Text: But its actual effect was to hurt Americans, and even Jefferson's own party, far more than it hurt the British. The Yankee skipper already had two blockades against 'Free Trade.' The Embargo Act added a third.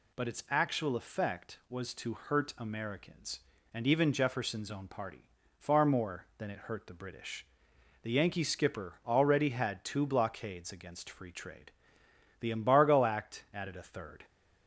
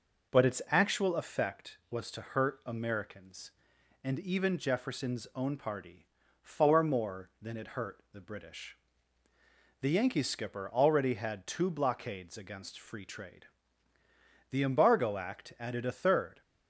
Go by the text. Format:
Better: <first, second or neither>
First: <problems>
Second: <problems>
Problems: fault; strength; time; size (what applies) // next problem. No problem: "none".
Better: neither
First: none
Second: none